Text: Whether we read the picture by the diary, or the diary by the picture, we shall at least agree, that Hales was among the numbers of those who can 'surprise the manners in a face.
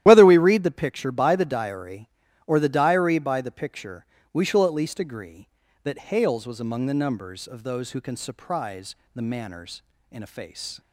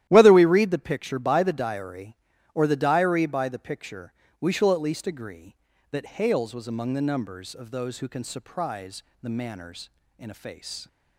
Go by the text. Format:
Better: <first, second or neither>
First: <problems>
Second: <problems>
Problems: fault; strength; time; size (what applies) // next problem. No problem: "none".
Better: second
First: loses the start of "Whether"; at 0.0 s; 40 ms // starts louder than the rest; strong; until 1.0 s; 13 dB // pauses between "surprise" and "the"; slight; at 8.9 s; 0.18 s long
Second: starts louder than the rest; strong; until 1.1 s; 13 dB // pauses between "surprise" and "the"; slight; at 9.0 s; 0.18 s long